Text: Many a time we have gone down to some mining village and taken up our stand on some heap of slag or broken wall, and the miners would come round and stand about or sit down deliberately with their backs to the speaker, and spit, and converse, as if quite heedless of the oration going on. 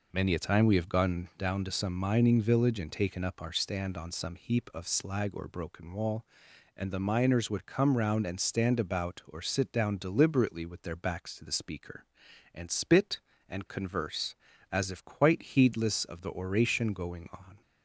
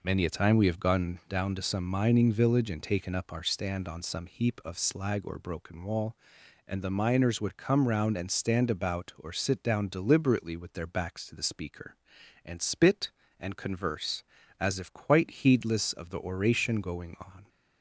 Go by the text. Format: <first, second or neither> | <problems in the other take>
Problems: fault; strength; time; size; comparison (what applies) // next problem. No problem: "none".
neither | none